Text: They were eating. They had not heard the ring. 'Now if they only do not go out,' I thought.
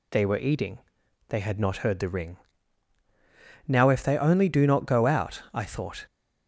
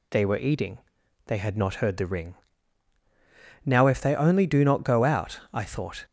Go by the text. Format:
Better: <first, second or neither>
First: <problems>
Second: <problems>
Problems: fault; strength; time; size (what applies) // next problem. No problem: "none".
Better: neither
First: none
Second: none